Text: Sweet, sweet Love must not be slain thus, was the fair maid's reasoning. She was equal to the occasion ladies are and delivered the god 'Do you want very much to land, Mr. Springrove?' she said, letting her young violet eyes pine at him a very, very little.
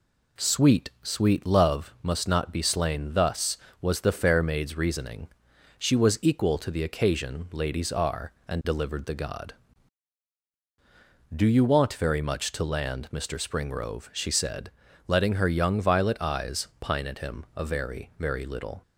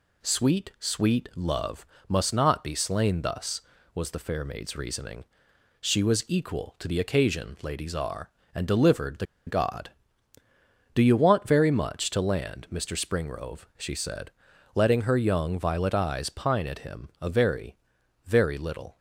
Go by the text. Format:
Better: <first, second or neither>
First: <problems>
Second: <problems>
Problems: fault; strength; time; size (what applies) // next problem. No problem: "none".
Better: first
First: none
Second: pauses between "Love" and "must"; slight; at 1.8 s; 0.24 s long // pauses between "the" and "god"; slight; at 9.2 s; 0.21 s long